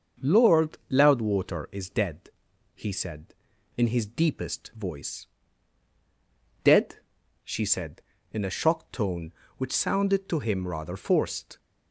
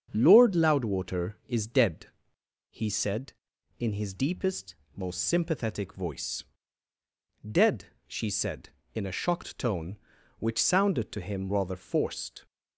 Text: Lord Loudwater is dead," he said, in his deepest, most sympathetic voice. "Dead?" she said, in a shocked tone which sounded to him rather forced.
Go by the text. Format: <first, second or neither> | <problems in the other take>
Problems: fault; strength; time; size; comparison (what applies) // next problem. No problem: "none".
second | starts louder than the rest; until 1.3 s; 6.5 dB; strong in the second // skips "most sympathetic"; at 4.7 s